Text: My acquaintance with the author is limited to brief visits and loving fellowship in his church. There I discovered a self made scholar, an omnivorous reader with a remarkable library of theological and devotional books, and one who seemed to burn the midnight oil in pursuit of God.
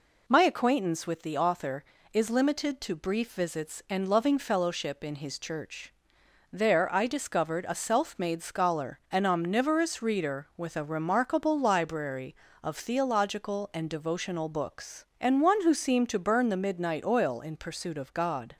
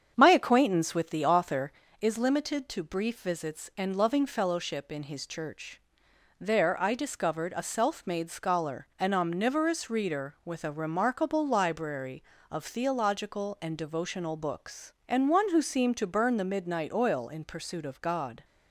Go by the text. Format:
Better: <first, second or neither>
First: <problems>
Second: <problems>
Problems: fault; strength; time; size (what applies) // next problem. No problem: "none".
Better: first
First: none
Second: starts louder than the rest; strong; until 1.9 s; 7.5 dB